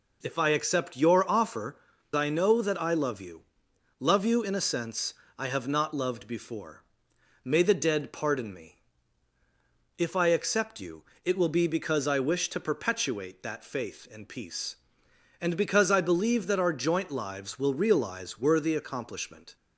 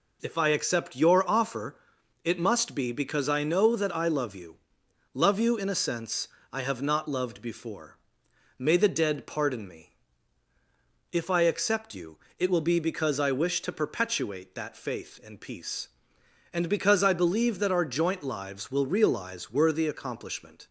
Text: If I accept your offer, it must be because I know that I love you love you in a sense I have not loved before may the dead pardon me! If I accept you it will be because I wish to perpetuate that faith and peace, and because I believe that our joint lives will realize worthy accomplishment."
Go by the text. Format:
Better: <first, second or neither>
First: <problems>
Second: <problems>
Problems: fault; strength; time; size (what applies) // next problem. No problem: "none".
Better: second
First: skips "it must be because"; at 1.9 s // pauses between "you" and "love"; noticeable; at 3.4 s; 0.56 s long // pauses between "sense" and "I"; slight; at 5.1 s; 0.24 s long // pauses between "before" and "may"; noticeable; at 6.8 s; 0.60 s long // pauses between "you" and "it"; slight; at 11.0 s; 0.20 s long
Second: pauses between "you" and "love"; noticeable; at 4.5 s; 0.56 s long // pauses between "sense" and "I"; slight; at 6.2 s; 0.24 s long // pauses between "before" and "may"; noticeable; at 7.9 s; 0.60 s long // pauses between "you" and "it"; slight; at 12.1 s; 0.20 s long